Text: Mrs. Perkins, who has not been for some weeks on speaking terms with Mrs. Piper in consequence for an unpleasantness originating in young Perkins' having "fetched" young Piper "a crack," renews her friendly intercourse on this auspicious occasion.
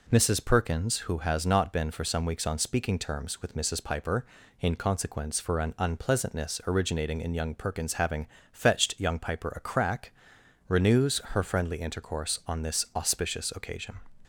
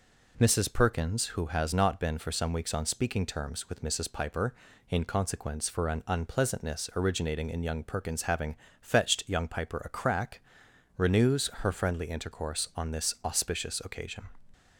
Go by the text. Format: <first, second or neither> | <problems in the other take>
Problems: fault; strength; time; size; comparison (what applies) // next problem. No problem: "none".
neither | pauses between "having" and "fetched"; slight; the same in both